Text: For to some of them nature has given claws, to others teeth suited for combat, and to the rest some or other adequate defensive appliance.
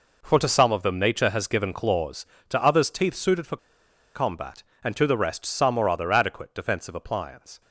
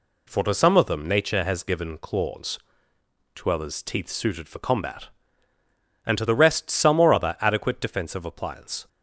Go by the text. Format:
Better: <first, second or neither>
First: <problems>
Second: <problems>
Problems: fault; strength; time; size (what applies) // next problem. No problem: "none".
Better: second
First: pauses between "for" and "combat"; noticeable; at 3.5 s; 0.58 s long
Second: none